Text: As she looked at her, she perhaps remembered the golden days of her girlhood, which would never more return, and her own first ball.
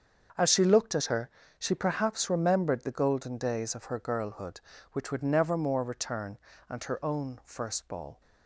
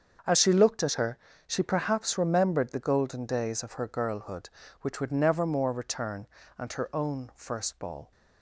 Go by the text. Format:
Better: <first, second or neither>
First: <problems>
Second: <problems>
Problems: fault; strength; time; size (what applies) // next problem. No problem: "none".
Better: neither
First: starts louder than the rest; until 1.6 s; 6.5 dB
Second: starts louder than the rest; until 1.5 s; 6.5 dB